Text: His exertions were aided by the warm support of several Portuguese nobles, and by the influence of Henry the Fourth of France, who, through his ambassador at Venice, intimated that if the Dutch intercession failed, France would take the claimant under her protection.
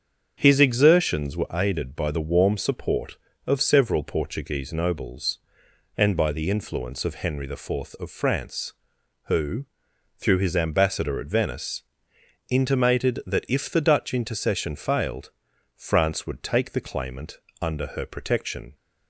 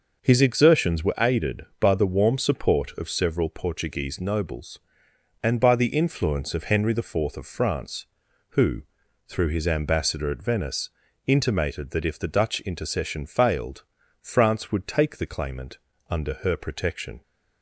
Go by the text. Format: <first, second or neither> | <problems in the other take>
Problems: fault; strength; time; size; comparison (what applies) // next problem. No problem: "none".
neither | starts louder than the rest; the same in both // pauses between "claimant" and "under"; slight; the same in both